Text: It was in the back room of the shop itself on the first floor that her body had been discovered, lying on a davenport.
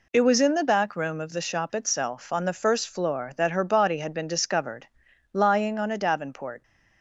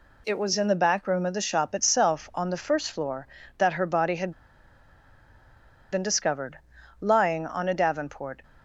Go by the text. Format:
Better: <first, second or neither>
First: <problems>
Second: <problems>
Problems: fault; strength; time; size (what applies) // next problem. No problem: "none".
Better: first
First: none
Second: pauses between "had" and "been"; strong; at 4.3 s; 1.6 s long